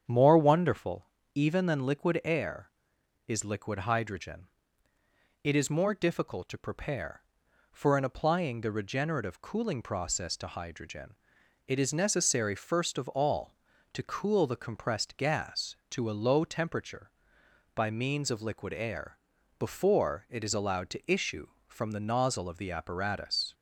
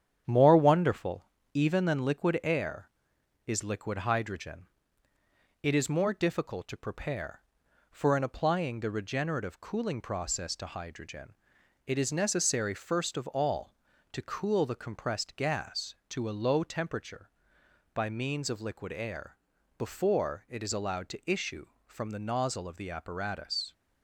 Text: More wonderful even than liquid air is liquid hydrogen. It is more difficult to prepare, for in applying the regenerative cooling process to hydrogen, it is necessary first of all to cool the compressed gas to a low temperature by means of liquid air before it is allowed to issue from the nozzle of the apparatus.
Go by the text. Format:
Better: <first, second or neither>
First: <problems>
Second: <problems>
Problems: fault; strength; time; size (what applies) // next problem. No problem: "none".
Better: first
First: starts louder than the rest; strong; until 1.3 s; 8.5 dB // pauses between "wonderful" and "even"; slight; at 1.0 s; 0.28 s long // pauses between "air" and "before"; at 19.1 s; 0.40 s long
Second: gets quieter; throughout; 4 dB // starts louder than the rest; strong; until 1.5 s; 9 dB // pauses between "wonderful" and "even"; slight; at 1.2 s; 0.28 s long // pauses between "air" and "before"; at 19.3 s; 0.40 s long